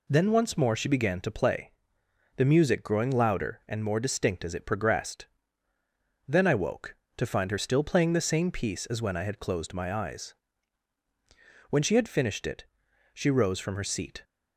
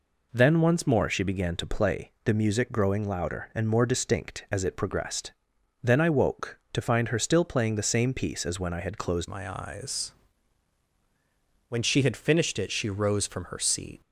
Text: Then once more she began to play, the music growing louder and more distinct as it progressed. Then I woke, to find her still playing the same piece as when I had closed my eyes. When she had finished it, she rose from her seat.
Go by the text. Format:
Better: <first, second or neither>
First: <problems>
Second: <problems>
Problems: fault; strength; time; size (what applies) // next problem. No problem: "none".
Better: first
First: none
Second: changes voice at "my"; from 9.2 s on; 4.8 s long